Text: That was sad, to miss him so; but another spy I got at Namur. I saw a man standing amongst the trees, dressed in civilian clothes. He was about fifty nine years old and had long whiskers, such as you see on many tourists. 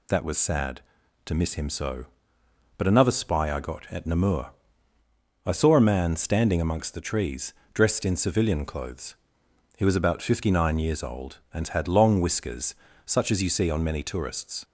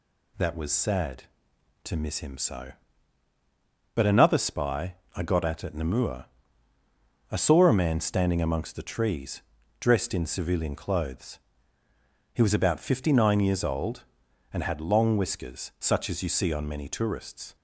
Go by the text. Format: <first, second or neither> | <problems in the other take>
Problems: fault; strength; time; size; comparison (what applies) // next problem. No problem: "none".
first | pauses between "spy" and "I"; slight; at 4.9 s; 0.18 s long // says "at" twice; at 5.6 s